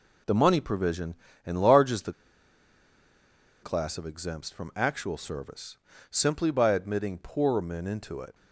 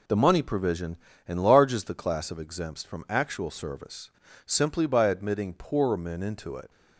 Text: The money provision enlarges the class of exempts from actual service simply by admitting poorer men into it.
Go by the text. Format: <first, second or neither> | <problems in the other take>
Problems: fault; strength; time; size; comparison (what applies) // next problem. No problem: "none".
second | pauses between "provision" and "enlarges"; slight; at 1.1 s; 0.28 s long; slight in the second // pauses between "the" and "class"; strong; at 2.1 s; 1.5 s long // pauses between "service" and "simply"; slight; at 5.7 s; 0.34 s long; also in the second